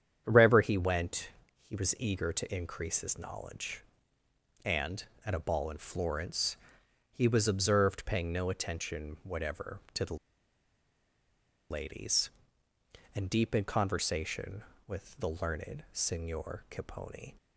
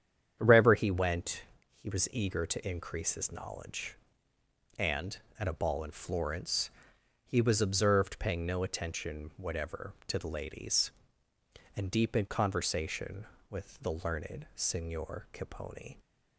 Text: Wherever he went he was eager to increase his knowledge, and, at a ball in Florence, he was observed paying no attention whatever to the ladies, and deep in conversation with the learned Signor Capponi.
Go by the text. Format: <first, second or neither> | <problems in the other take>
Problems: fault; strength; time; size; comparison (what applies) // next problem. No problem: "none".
second | starts louder than the rest; strong; until 1.2 s; 8.5 dB; strong in the second // pauses between "went" and "he"; slight; at 1.2 s; 0.32 s long; slight in the second // pauses between "the" and "ladies"; strong; at 10.1 s; 1.5 s long